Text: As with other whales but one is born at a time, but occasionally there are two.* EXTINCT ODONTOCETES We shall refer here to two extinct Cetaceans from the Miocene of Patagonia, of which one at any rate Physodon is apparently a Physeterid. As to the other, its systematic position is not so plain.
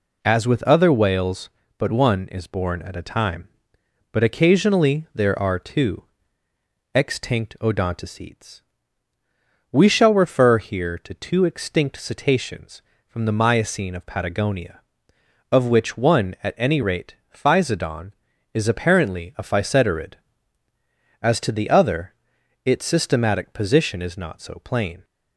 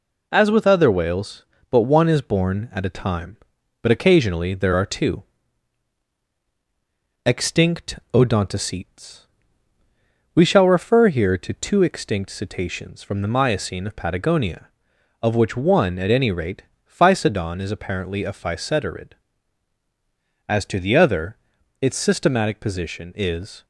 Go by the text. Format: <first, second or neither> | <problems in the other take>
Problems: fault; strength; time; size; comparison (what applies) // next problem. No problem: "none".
first | pauses between "EXTINCT" and "ODONTOCETES"; slight; at 7.9 s; 0.16 s long // pauses between "ODONTOCETES" and "We"; at 9.2 s; 1.1 s long; also in the first // pauses between "rate" and "Physodon"; slight; at 16.6 s; 0.24 s long; slight in the first // stops before "not so plain"; at 23.6 s